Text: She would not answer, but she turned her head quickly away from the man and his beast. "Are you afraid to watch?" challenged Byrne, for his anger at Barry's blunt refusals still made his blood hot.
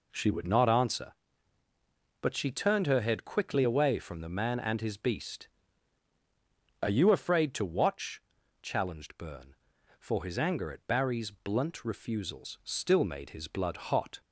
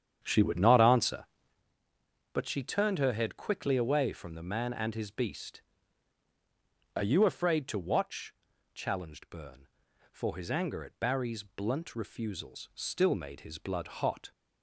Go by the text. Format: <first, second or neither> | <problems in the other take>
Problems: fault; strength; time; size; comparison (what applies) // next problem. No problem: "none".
first | starts louder than the rest; strong; until 1.6 s; 9 dB